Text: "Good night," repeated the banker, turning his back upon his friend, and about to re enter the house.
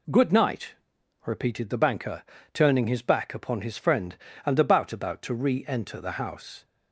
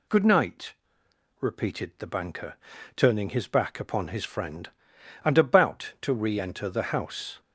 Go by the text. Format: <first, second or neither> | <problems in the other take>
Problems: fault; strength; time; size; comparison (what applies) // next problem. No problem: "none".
second | says "about" twice; at 4.9 s